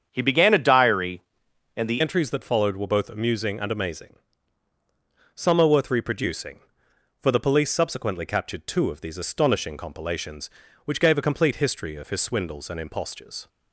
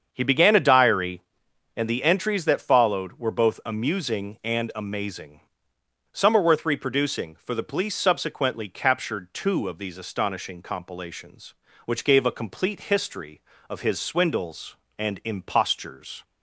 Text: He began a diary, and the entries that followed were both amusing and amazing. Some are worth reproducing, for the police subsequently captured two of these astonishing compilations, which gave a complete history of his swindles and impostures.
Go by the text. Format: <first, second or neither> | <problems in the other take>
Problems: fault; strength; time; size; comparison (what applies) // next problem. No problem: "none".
second | starts louder than the rest; strong; until 1.1 s; 8 dB; strong in the second // changes voice at "entries"; from 2.0 s on; 11.4 s long